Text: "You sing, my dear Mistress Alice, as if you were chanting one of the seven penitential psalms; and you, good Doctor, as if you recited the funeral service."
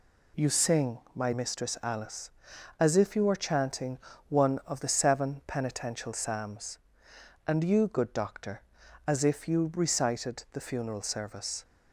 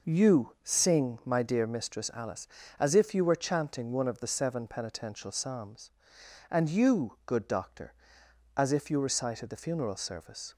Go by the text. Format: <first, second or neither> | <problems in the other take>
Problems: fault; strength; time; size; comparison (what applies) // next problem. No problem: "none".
second | skips "dear"; at 1.3 s // pauses between "chanting" and "one"; slight; at 3.9 s; 0.28 s long